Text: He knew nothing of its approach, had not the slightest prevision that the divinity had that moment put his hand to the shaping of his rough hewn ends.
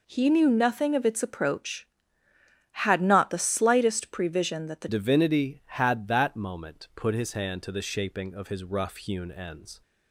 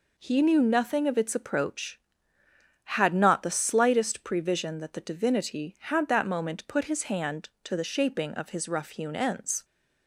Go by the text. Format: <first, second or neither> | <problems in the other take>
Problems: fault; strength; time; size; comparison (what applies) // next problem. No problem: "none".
second | changes voice at "divinity"; from 4.8 s on; 5.0 s long